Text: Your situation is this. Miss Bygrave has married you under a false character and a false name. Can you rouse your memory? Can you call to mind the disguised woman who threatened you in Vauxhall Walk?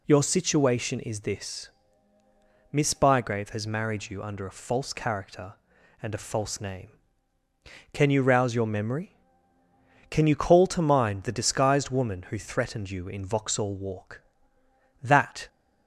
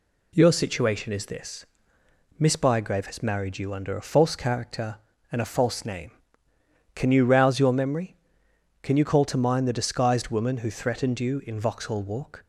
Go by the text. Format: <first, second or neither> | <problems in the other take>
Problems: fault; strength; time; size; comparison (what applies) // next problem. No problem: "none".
second | goes on to say "That"; slight; from 15.0 s on; 0.46 s long